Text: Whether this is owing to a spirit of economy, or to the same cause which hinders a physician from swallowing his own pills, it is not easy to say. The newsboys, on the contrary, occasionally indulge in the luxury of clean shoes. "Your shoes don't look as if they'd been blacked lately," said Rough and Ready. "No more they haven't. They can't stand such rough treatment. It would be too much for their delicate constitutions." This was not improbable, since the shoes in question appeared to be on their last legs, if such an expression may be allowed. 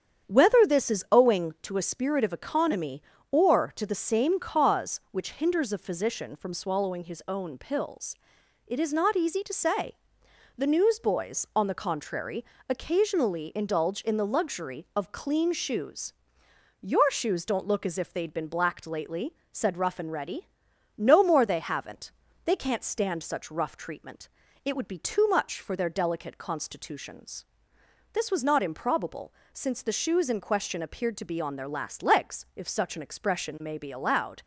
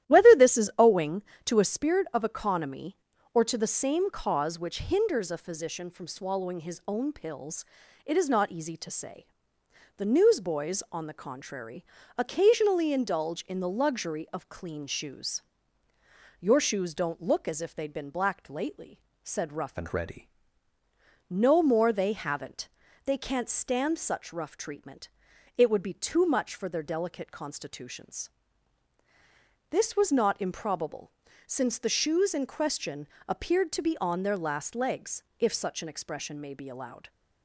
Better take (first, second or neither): first